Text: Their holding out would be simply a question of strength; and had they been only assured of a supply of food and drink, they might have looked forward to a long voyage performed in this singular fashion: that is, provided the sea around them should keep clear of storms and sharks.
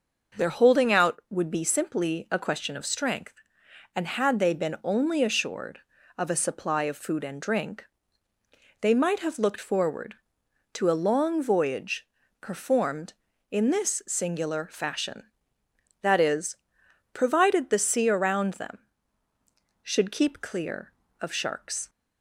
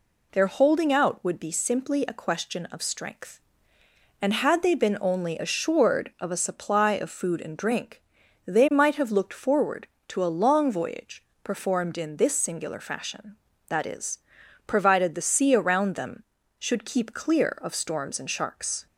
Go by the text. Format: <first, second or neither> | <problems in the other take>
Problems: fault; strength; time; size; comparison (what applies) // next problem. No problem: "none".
second | pauses between "voyage" and "performed"; slight; at 12.0 s; 0.34 s long; slight in the second // skips "storms and"; at 21.3 s